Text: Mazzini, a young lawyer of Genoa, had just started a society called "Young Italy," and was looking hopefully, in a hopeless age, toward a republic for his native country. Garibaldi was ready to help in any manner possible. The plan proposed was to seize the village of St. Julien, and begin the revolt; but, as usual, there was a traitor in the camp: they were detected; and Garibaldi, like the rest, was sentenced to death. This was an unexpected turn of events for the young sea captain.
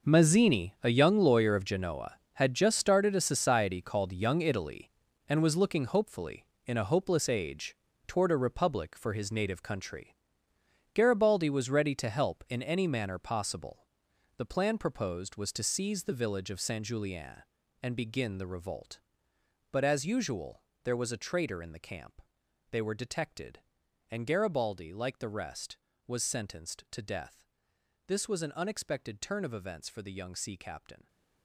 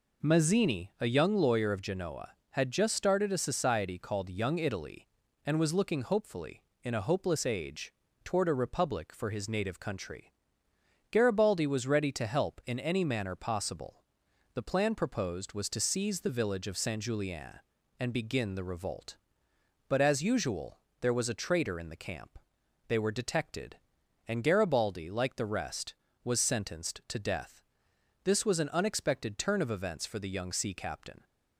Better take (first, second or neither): second